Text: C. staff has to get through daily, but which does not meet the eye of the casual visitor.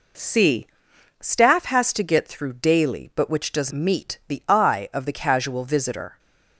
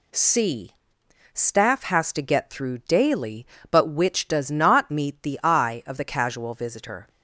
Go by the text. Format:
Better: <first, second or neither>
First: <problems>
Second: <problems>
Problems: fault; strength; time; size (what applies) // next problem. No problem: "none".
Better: second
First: skips "not"; at 3.7 s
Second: none